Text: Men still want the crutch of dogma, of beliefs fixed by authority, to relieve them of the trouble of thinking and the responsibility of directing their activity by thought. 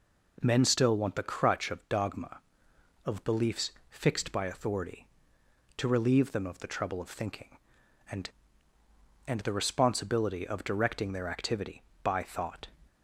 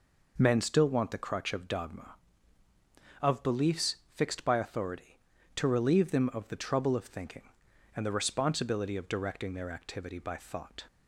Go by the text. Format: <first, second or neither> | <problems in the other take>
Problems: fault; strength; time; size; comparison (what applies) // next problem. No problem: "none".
second | pauses between "beliefs" and "fixed"; slight; at 3.7 s; 0.18 s long; slight in the second // says "and" twice; at 9.2 s